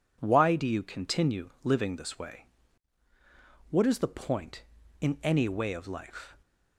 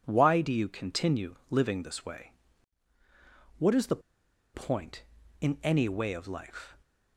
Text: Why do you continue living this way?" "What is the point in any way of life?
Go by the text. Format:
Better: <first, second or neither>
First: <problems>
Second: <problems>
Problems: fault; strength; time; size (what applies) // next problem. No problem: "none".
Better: first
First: none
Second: pauses between "continue" and "living"; slight; at 1.3 s; 0.16 s long // pauses between "the" and "point"; noticeable; at 4.0 s; 0.53 s long